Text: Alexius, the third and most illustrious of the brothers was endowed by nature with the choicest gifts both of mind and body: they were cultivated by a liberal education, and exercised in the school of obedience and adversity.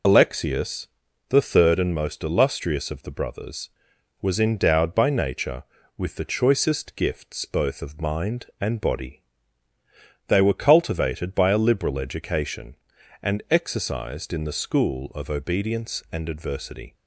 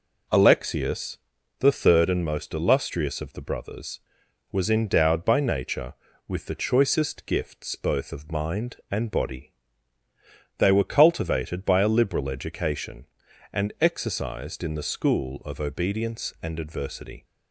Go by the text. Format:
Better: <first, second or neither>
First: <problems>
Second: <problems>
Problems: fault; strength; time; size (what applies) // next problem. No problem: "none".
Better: second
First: loses the start of "Alexius"; at 0.0 s; 55 ms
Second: none